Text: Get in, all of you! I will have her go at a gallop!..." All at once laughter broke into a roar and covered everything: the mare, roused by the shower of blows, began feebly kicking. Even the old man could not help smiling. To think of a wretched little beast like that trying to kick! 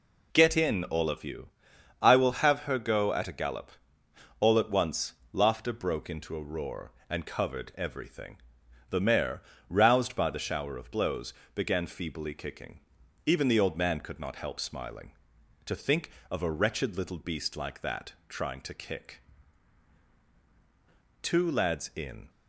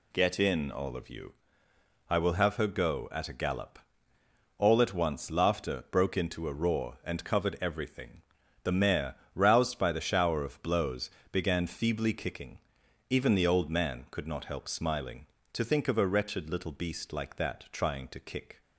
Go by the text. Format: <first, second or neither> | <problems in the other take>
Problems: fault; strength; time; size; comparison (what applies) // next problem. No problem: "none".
second | pauses between "once" and "laughter"; slight; at 5.1 s; 0.18 s long // goes on to say "Two lads in"; noticeable; from 21.2 s on; 1.0 s long